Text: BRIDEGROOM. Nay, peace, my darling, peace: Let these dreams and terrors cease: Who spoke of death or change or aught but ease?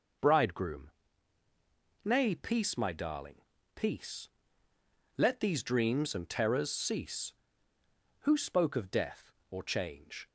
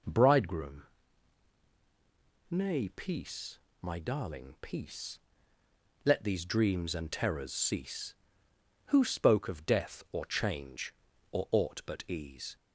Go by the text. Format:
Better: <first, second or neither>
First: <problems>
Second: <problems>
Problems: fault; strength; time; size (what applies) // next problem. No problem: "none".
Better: second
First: stops before "or aught but ease"; at 10.2 s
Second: none